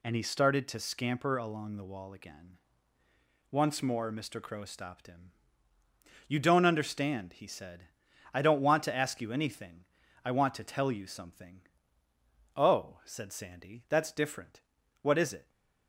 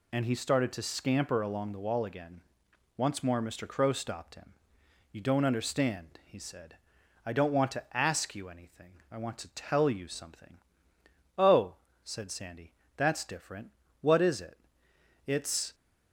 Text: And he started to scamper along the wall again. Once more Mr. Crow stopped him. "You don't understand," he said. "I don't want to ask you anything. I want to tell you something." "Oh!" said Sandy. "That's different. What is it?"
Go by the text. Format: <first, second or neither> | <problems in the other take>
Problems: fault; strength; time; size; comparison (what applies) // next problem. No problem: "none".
first | goes on to say "It's"; slight; from 15.2 s on; 0.48 s long